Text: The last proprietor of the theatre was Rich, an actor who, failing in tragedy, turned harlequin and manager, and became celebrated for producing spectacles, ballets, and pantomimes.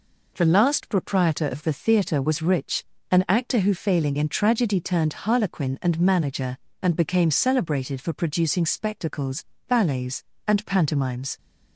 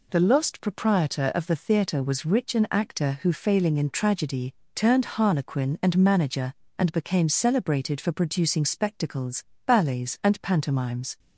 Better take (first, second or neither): first